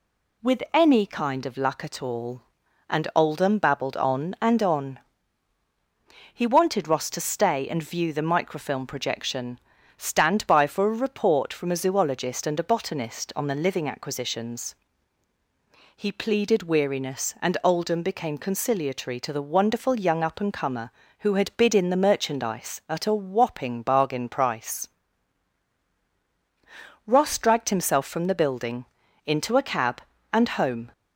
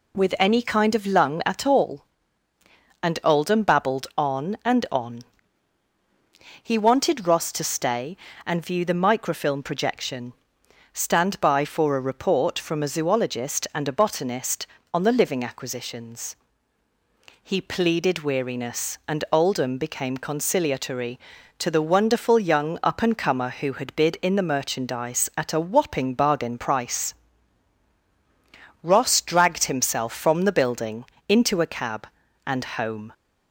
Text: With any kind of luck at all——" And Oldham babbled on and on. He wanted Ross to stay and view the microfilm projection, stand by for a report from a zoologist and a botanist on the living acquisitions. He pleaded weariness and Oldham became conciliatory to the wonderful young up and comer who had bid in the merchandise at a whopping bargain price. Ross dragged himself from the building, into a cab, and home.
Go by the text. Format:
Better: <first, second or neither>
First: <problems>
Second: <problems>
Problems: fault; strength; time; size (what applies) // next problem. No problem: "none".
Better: first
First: none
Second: says "lung" for "luck"; at 1.0 s